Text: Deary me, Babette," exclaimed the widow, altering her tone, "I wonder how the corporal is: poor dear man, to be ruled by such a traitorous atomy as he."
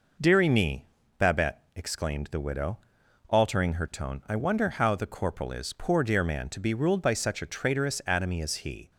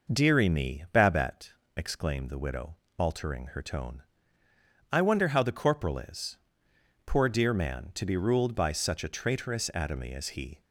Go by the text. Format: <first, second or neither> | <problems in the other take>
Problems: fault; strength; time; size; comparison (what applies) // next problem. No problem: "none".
neither | none